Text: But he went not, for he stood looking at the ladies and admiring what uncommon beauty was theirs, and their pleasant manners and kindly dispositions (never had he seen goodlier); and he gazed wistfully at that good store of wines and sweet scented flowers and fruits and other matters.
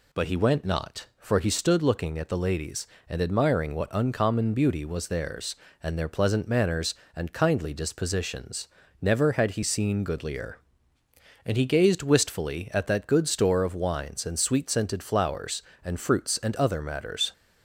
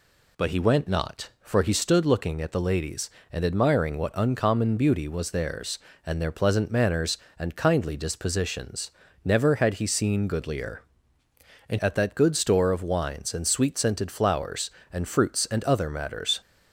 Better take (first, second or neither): first